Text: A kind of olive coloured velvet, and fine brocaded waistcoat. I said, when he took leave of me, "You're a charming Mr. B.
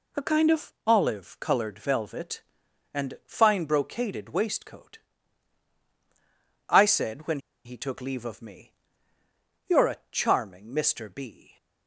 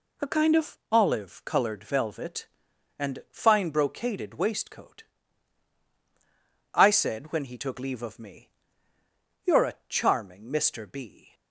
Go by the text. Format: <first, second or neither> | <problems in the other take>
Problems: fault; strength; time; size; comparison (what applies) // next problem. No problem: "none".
second | pauses between "when" and "he"; slight; at 7.3 s; 0.26 s long